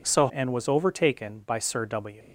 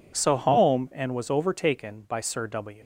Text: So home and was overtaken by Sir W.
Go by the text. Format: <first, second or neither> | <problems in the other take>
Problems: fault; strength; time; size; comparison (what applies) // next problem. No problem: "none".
second | skips "home"; at 0.2 s